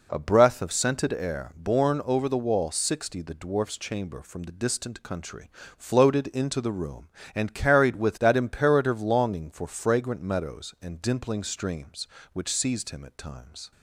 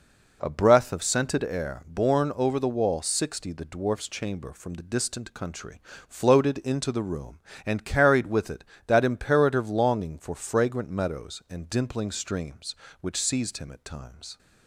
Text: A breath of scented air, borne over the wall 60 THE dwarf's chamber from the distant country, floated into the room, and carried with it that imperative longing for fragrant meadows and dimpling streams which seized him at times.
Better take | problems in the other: second | skips "it"; at 8.1 s

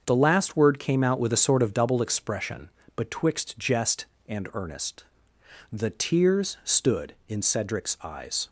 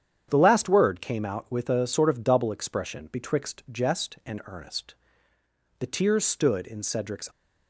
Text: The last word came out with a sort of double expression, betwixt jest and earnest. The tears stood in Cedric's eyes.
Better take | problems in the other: first | starts louder than the rest; strong; until 1.3 s; 8.5 dB; also in the first // stops before "eyes"; at 7.3 s

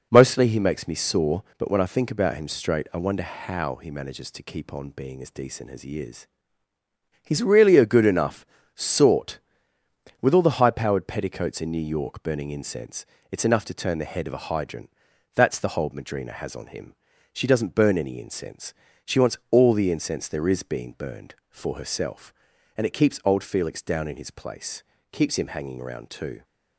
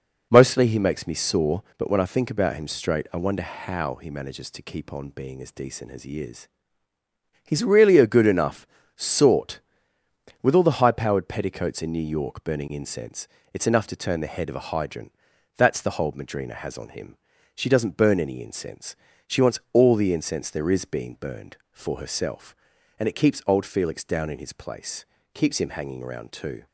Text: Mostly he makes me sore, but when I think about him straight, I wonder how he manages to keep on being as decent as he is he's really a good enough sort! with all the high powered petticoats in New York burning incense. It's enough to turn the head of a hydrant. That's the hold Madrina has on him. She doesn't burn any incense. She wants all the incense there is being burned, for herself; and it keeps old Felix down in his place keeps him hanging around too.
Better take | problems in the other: neither | pauses between "is" and "he's"; noticeable; the same in both // pauses between "enough" and "sort"; slight; the same in both // pauses between "place" and "keeps"; slight; the same in both

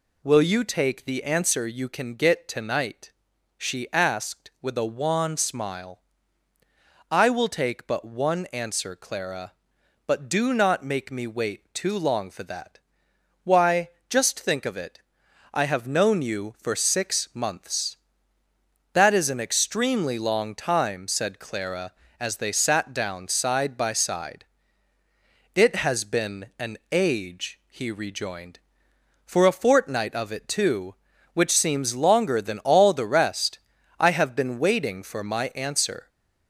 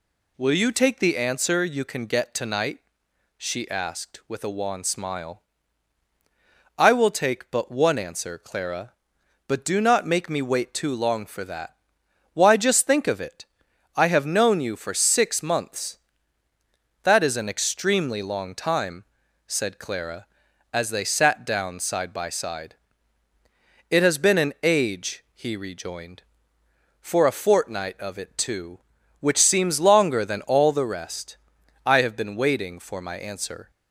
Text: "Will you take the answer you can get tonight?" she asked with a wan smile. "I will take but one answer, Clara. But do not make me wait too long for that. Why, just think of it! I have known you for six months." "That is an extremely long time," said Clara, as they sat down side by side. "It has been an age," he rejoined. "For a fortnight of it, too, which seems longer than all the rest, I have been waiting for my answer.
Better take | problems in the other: second | gets louder; slight; throughout; 3.5 dB

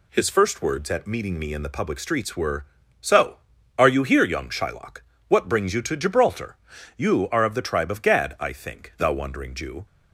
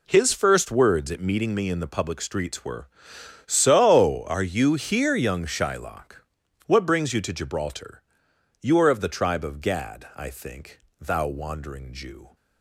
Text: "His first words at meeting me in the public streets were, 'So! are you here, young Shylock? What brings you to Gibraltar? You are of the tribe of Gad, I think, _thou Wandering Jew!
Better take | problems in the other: neither | none

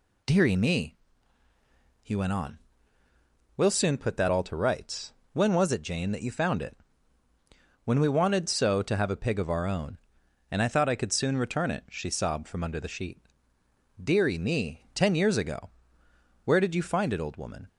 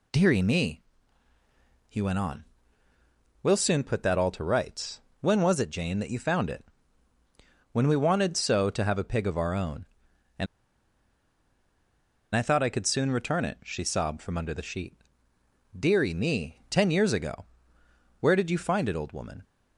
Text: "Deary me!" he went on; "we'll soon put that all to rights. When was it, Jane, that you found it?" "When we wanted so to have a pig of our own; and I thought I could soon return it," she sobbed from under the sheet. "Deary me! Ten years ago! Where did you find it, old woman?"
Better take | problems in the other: first | pauses between "and" and "I"; strong; at 10.4 s; 1.8 s long

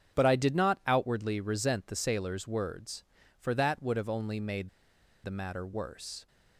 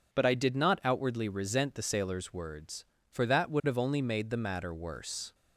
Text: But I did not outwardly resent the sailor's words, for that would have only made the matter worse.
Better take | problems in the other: second | starts louder than the rest; strong; until 1.2 s; 8 dB // pauses between "made" and "the"; noticeable; at 4.6 s; 0.55 s long

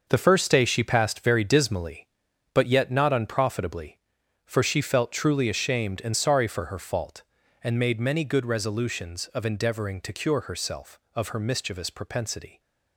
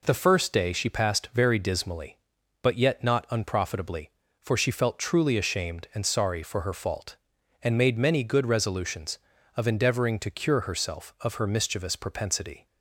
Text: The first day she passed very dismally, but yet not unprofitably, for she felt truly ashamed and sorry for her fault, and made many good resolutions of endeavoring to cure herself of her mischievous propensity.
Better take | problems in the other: second | gets quieter; strong; throughout; 9 dB

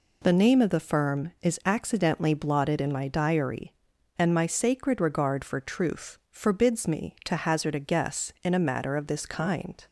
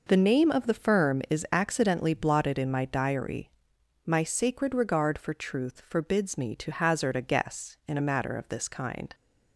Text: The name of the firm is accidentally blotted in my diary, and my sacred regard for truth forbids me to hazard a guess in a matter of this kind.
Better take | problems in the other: first | skips "and"; at 3.7 s

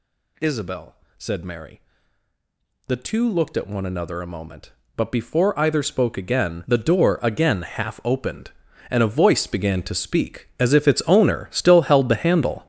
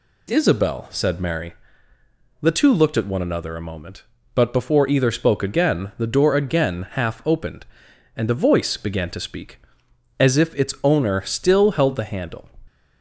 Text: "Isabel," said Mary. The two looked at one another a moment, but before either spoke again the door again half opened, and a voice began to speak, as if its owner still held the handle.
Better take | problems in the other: second | gets louder; strong; throughout; 10.5 dB

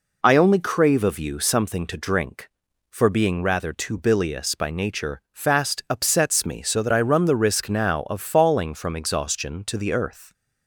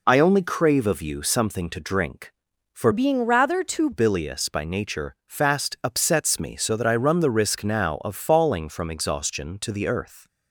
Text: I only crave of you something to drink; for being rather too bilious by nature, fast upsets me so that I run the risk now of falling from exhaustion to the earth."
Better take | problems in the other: first | changes voice from "being" to "too"; from 2.9 to 3.9 s; 1.0 s long

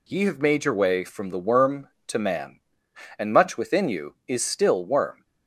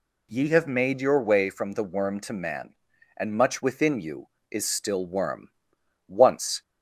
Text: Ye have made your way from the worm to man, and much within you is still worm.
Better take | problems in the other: first | goes on to say "Once"; from 6.0 s on; 0.54 s long

